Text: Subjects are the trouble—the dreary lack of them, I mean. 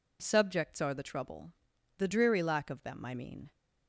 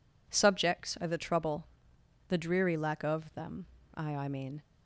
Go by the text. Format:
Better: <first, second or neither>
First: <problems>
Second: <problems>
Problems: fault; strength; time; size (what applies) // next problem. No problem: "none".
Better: first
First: none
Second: says "I" twice; at 4.1 s